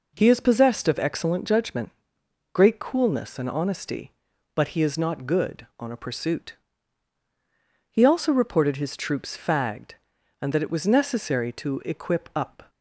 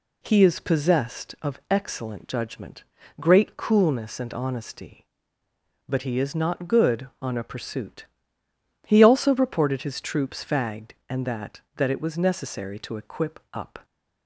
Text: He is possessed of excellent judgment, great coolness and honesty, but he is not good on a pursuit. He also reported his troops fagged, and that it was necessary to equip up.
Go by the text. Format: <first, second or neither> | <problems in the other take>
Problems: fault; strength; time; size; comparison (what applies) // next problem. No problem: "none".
first | says "that" twice; at 11.7 s